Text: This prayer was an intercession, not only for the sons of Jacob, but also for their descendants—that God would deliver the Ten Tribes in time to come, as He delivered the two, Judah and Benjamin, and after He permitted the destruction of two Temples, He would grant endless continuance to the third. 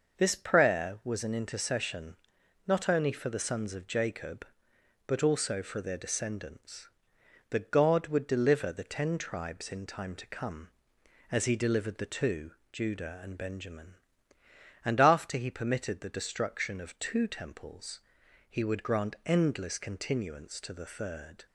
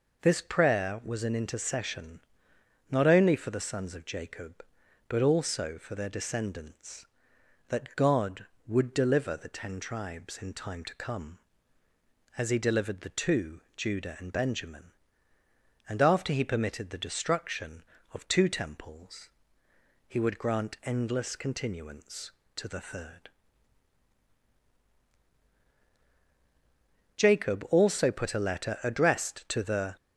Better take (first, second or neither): first